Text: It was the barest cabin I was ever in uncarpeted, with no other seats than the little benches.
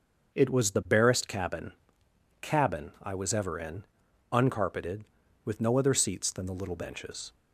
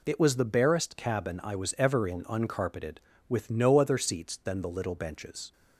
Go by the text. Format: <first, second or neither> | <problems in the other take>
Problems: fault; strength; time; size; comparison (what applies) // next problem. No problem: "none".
second | starts louder than the rest; until 1.3 s; 6.5 dB // says "cabin" twice; at 2.4 s // pauses between "in" and "uncarpeted"; noticeable; at 3.8 s; 0.48 s long